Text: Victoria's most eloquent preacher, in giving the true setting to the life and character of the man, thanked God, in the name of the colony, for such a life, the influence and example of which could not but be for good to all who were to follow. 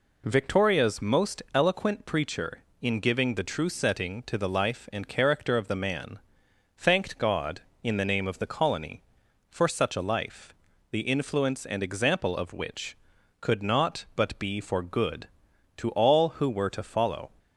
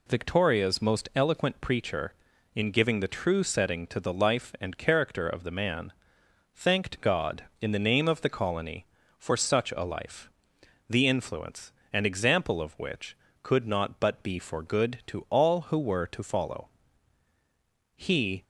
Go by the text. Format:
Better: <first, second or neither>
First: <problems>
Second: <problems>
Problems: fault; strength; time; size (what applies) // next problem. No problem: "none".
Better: first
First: none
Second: goes on to say "He"; slight; from 17.9 s on; 0.48 s long